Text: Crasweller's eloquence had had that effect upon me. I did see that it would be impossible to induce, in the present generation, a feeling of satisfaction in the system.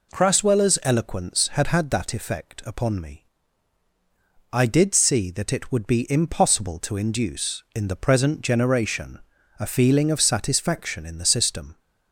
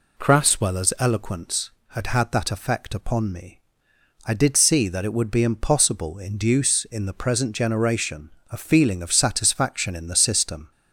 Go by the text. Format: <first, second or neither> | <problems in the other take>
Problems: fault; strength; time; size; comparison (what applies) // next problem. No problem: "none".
first | skips "to"; at 6.1 s